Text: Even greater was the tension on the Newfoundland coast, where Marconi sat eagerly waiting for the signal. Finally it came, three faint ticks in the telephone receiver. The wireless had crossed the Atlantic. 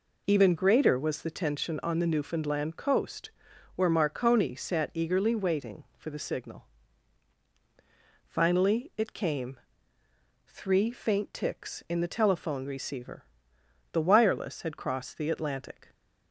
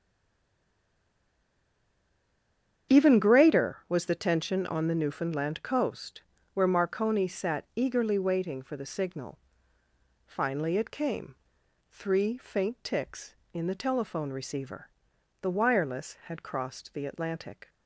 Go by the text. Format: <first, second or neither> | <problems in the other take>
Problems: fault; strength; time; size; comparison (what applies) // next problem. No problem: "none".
first | stays silent before the first word; strong; until 2.9 s; 2.9 s long // starts louder than the rest; strong; until 4.0 s; 8.5 dB